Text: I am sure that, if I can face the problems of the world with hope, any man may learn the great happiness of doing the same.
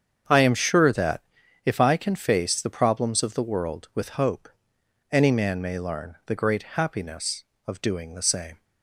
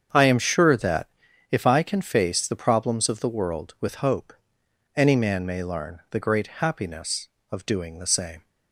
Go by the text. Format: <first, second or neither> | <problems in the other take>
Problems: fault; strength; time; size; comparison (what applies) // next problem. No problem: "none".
neither | starts louder than the rest; strong; the same in both